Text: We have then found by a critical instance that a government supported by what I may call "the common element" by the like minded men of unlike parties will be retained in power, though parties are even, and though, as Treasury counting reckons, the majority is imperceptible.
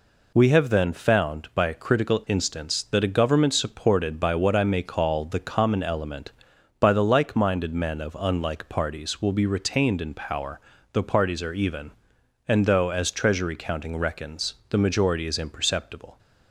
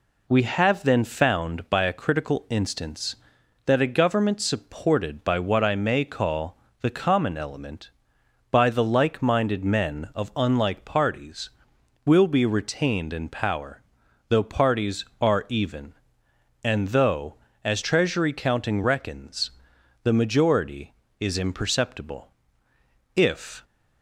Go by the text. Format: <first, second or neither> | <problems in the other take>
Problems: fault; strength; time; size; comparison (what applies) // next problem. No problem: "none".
first | pauses between "call" and "the"; slight; at 6.5 s; 0.24 s long // goes on to say "If"; slight; from 23.1 s on; 0.48 s long